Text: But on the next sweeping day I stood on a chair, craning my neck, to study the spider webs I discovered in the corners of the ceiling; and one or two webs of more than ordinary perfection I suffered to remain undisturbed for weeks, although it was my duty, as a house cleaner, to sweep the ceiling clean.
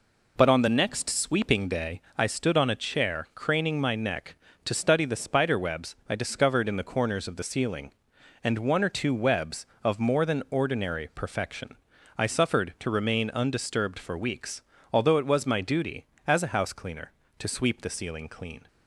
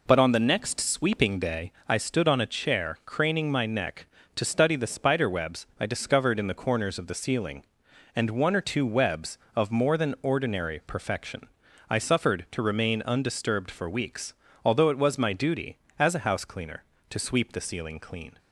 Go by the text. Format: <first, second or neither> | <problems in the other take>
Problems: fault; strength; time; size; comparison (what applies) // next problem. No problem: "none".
neither | pauses between "day" and "I"; slight; the same in both // pauses between "perfection" and "I"; the same in both